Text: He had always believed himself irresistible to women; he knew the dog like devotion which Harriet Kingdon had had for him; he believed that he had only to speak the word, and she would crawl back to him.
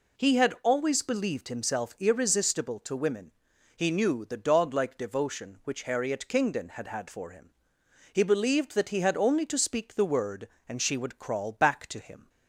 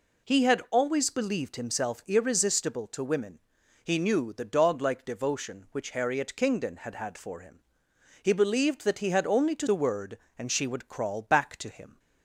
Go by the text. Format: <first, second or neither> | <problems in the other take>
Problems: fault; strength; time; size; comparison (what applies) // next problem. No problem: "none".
first | skips "speak"; at 9.6 s